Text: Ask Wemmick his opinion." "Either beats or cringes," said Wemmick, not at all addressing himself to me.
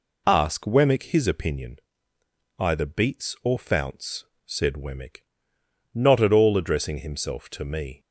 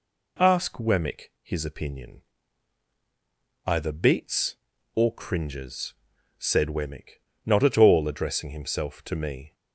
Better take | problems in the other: second | says "founts" for "cringes"; at 3.5 s

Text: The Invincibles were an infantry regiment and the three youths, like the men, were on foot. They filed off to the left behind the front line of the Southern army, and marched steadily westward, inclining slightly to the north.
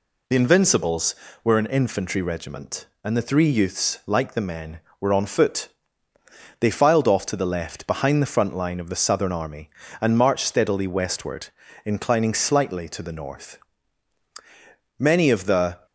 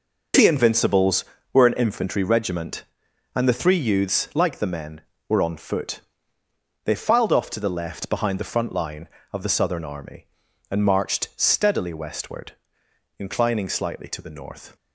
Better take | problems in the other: second | goes on to say "Many of the"; noticeable; from 14.9 s on; 0.88 s long

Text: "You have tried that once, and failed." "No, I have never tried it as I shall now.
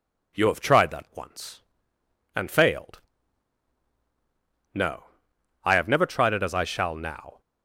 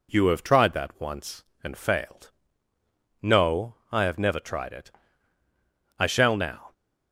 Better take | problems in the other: first | skips "as"; at 5.4 s

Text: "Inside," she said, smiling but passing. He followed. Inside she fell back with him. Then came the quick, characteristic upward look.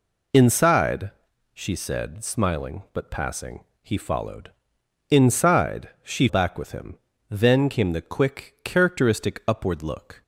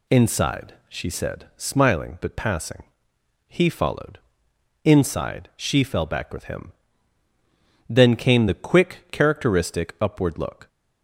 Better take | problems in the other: second | skips "fell"; at 6.2 s

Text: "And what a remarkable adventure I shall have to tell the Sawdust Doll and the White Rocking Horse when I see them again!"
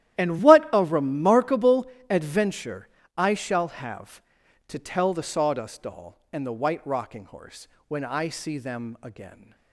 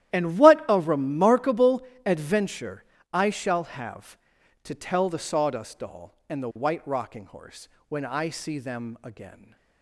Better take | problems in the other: neither | starts louder than the rest; strong; the same in both // pauses between "remarkable" and "adventure"; slight; the same in both // pauses between "adventure" and "I"; slight; the same in both // pauses between "Horse" and "when"; slight; the same in both

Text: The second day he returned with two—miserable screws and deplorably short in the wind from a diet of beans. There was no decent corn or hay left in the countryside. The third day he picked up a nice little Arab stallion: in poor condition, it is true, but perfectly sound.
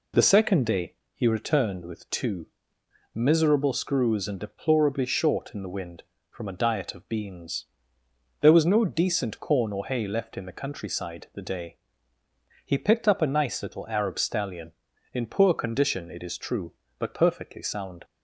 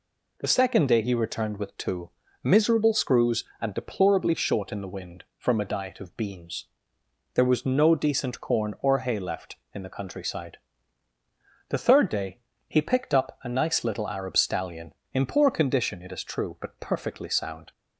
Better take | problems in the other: second | pauses between "day" and "he"; slight; at 0.9 s; 0.20 s long // skips "third"; at 11.4 s // pauses between "day" and "he"; noticeable; at 11.7 s; 0.90 s long; slight in the second

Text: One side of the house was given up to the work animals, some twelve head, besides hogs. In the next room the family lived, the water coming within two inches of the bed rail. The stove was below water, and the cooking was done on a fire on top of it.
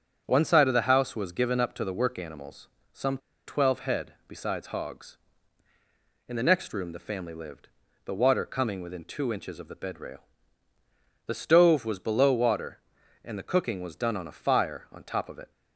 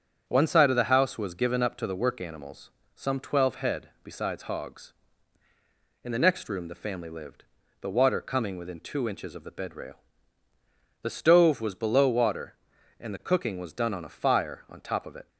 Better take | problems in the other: second | starts louder than the rest; strong; until 1.2 s; 8 dB; strong in the second // pauses between "some" and "twelve"; slight; at 3.1 s; 0.28 s long

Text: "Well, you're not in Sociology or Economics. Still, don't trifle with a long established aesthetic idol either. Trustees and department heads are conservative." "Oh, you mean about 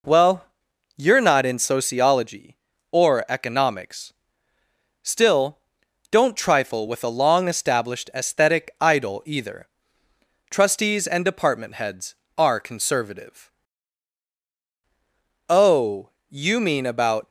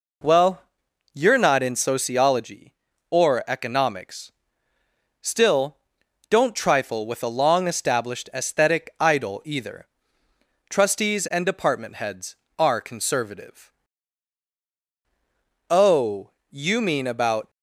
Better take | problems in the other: neither | none

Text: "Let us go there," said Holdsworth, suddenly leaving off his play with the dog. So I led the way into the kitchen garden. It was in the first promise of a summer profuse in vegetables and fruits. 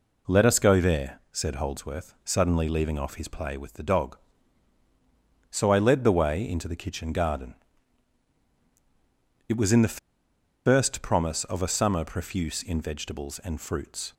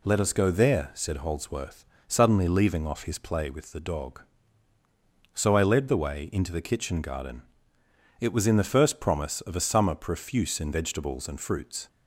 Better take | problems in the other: second | pauses between "the" and "first"; noticeable; at 9.9 s; 0.68 s long

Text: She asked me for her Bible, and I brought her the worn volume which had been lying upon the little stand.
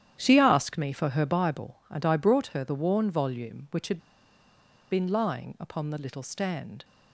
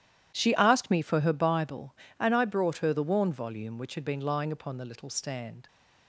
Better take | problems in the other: second | starts louder than the rest; strong; until 1.2 s; 10.5 dB; strong in the second // pauses between "had" and "been"; noticeable; at 3.9 s; 0.94 s long

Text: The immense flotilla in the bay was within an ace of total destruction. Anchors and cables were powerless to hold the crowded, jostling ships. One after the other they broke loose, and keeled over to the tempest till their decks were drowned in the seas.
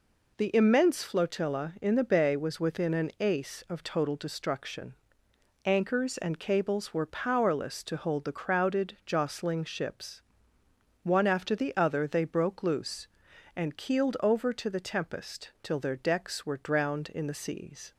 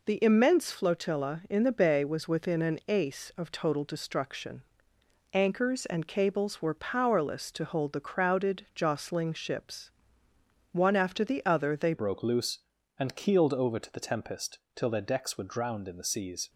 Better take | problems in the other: first | changes voice at "broke"; from 11.9 s on; 4.5 s long // pauses between "tempest" and "till"; slight; at 14.5 s; 0.16 s long

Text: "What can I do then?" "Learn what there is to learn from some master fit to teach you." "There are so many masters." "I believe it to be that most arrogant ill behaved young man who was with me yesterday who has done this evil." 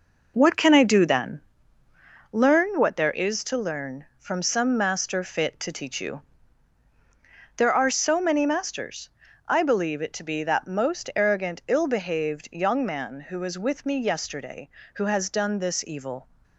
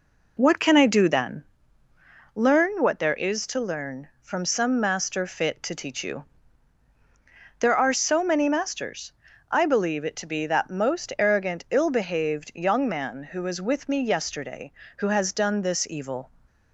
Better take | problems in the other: second | gets quieter; throughout; 6.5 dB

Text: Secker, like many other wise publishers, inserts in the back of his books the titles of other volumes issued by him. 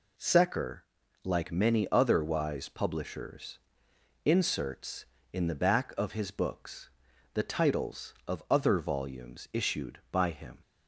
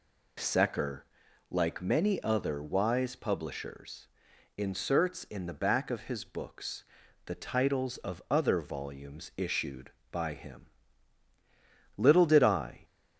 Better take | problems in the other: first | pauses between "books" and "the"; at 6.8 s; 0.40 s long; noticeable in the first // goes on to say "Little did I"; noticeable; from 11.9 s on; 0.88 s long

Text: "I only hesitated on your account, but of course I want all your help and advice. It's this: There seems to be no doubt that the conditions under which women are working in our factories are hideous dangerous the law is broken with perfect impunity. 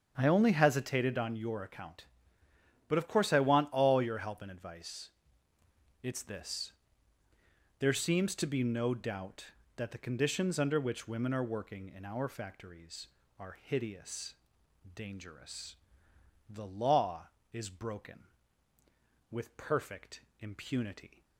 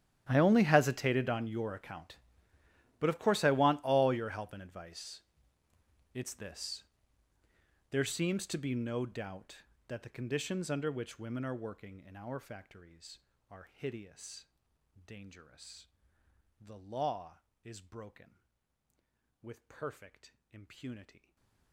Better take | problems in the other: first | gets quieter; strong; throughout; 24 dB // starts louder than the rest; strong; until 1.2 s; 11.5 dB; strong in the first // pauses between "hideous" and "dangerous"; noticeable; at 14.4 s; 0.60 s long; noticeable in the first // pauses between "dangerous" and "the"; noticeable; at 15.8 s; 0.72 s long; noticeable in the first // pauses between "perfect" and "impunity"; slight; at 20.3 s; 0.16 s long; slight in the first // stays silent after the last word; slight; from 21.1 s on; 0.6 s long

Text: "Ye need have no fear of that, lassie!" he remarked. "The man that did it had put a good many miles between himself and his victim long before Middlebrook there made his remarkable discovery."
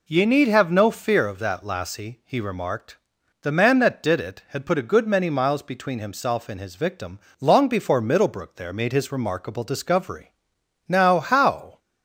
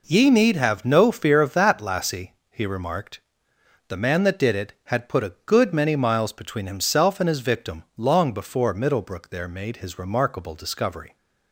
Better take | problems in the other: second | pauses between "victim" and "long"; slight; at 7.1 s; 0.22 s long // goes on to say "Now how"; noticeable; from 10.8 s on; 0.92 s long

